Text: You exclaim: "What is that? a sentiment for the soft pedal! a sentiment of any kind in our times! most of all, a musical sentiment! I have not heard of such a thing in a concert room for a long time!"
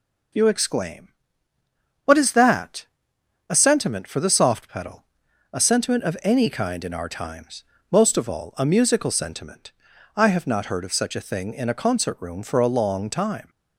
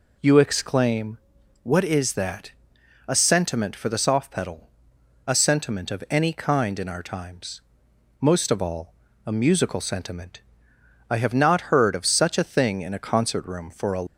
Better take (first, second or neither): first